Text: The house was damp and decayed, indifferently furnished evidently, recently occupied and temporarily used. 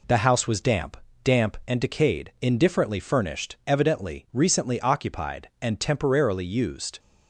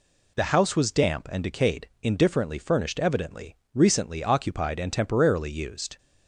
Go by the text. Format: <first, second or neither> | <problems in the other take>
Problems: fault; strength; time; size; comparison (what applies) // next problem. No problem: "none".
second | says "damp" twice; at 1.2 s